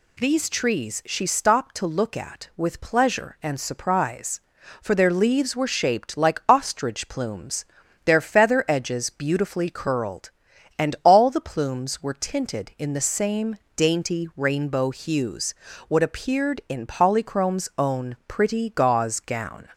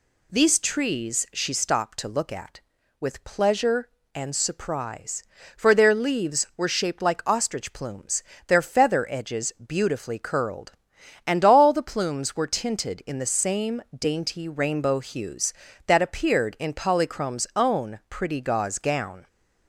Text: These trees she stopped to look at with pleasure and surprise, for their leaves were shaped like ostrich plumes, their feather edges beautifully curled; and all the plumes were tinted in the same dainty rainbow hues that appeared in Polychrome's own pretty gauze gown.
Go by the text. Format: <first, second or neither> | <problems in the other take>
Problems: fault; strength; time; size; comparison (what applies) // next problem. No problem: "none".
second | pauses between "same" and "dainty"; slight; at 13.5 s; 0.18 s long // says "what" for "that"; at 15.8 s